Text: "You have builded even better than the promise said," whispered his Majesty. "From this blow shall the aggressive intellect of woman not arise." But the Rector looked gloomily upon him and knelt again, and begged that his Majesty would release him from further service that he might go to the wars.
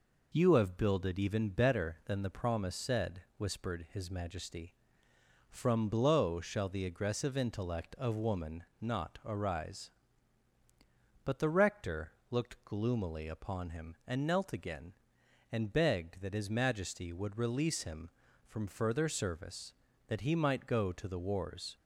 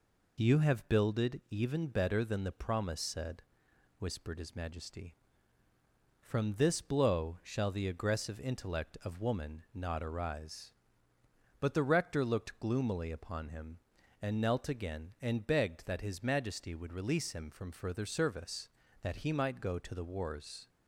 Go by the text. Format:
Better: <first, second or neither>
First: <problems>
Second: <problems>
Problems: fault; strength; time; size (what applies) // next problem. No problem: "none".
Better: second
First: skips "this"; at 5.8 s // pauses between "woman" and "not"; slight; at 8.6 s; 0.18 s long // pauses between "Rector" and "looked"; slight; at 12.1 s; 0.18 s long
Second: none